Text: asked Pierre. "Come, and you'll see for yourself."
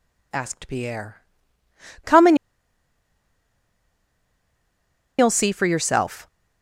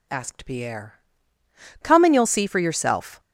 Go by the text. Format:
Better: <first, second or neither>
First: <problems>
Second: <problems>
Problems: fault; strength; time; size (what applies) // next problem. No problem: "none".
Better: second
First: pauses between "and" and "you'll"; strong; at 2.3 s; 2.8 s long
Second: none